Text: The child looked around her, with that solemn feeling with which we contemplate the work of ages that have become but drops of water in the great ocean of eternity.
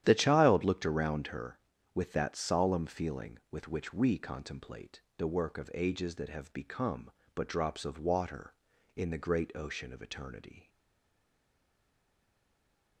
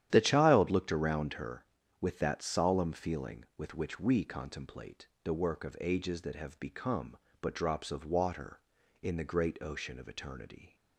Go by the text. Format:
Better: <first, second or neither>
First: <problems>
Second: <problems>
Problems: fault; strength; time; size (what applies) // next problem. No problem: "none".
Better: second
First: starts louder than the rest; strong; until 1.0 s; 10.5 dB // pauses between "contemplate" and "the"; slight; at 5.0 s; 0.16 s long // stays silent after the last word; from 10.6 s on; 2.4 s long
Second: starts louder than the rest; strong; until 1.1 s; 11 dB // pauses between "contemplate" and "the"; slight; at 5.0 s; 0.16 s long